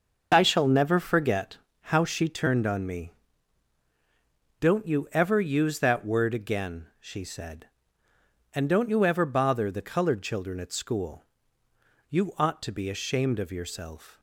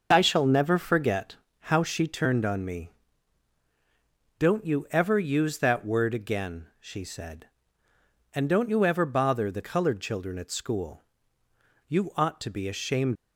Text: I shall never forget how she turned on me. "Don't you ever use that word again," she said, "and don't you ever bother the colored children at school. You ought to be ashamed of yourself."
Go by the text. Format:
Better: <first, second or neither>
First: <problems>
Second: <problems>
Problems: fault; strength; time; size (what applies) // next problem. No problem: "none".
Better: first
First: pauses between "forget" and "how"; slight; at 1.5 s; 0.22 s long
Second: pauses between "forget" and "how"; slight; at 1.3 s; 0.22 s long // stops before "of yourself"; at 13.1 s